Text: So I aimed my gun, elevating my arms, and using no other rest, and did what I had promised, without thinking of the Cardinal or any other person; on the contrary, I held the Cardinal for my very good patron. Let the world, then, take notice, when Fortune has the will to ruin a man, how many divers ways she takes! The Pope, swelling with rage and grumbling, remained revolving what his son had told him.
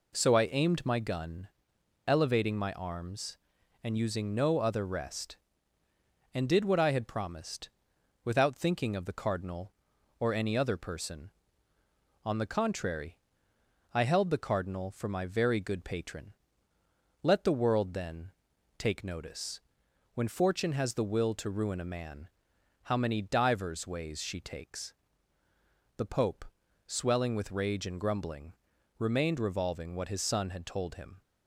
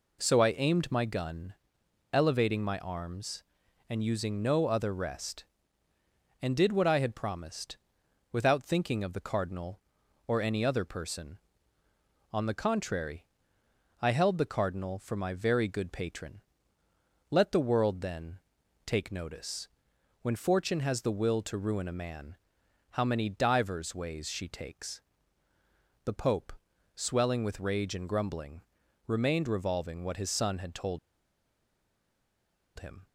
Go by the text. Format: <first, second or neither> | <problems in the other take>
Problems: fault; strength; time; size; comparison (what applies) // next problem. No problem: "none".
first | pauses between "told" and "him"; strong; at 30.9 s; 1.7 s long